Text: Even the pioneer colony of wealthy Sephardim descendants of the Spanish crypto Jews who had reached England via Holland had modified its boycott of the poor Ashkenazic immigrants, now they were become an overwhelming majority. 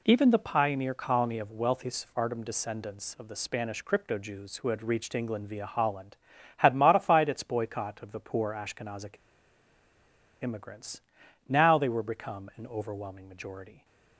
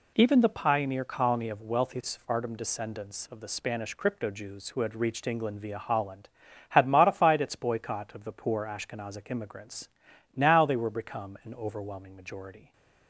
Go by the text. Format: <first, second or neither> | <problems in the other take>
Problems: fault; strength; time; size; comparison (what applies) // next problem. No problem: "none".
second | pauses between "Ashkenazic" and "immigrants"; strong; at 9.1 s; 1.2 s long